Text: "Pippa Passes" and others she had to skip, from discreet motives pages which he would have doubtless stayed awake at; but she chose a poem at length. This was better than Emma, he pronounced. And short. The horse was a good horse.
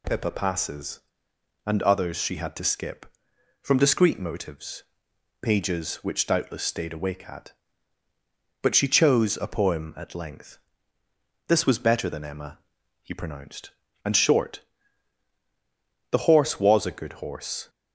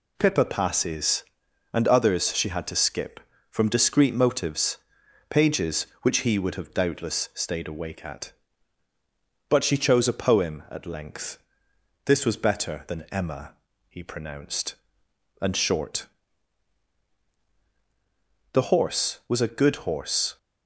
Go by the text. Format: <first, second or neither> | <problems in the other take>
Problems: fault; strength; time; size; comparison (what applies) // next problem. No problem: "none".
second | pauses between "motives" and "pages"; noticeable; at 4.8 s; 0.58 s long; noticeable in the second // skips "he would have"; at 6.2 s